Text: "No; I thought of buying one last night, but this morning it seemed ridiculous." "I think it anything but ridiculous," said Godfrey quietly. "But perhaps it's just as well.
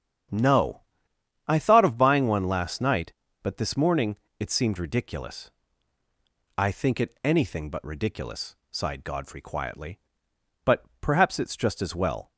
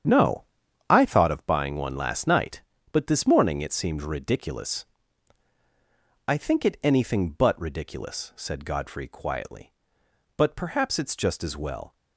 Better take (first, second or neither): second